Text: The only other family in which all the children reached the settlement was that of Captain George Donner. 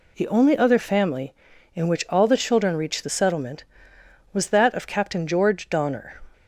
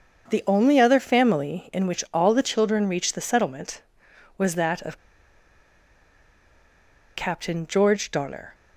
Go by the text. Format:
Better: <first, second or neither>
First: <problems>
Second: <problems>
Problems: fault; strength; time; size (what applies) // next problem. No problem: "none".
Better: first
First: none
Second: starts louder than the rest; until 1.3 s; 7 dB // pauses between "of" and "Captain"; strong; at 4.9 s; 2.1 s long